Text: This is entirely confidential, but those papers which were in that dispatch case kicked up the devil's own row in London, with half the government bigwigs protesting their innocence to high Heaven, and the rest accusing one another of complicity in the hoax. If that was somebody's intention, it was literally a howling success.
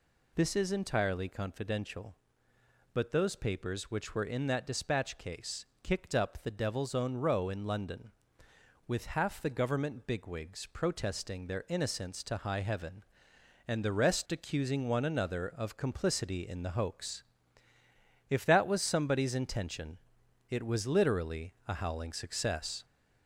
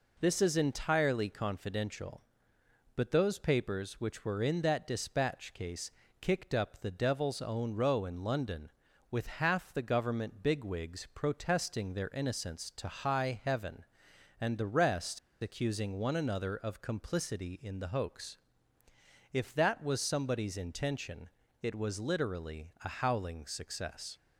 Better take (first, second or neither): first